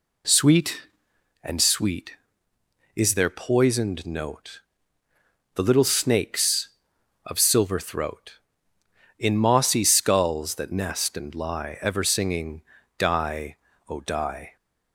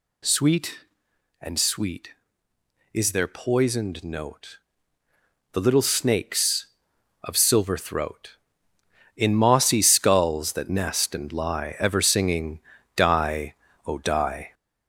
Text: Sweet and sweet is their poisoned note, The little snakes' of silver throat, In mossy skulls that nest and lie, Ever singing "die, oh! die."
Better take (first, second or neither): first